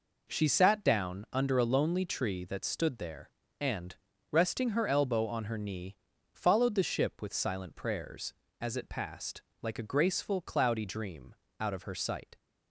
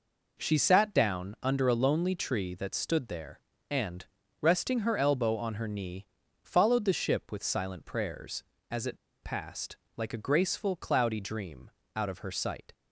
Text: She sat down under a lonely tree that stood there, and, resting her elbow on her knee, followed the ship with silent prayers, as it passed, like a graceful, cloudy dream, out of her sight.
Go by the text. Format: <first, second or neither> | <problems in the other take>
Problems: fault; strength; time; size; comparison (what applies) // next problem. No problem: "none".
first | pauses between "it" and "passed"; slight; at 8.9 s; 0.27 s long